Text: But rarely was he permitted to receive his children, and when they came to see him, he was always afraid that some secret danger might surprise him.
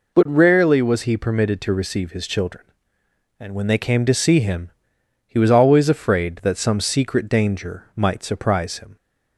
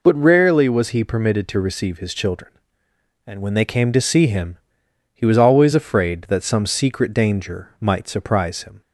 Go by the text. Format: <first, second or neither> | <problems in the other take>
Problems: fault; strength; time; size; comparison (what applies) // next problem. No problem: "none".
neither | none